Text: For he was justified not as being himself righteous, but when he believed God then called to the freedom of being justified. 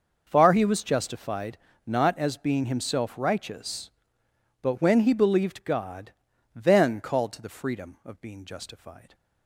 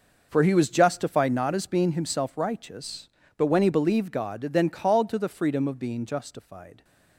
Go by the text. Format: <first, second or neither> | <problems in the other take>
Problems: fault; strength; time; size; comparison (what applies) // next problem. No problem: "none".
second | says "Far" for "For"; at 0.2 s // pauses between "justified" and "not"; slight; at 1.5 s; 0.30 s long // pauses between "God" and "then"; at 6.1 s; 0.42 s long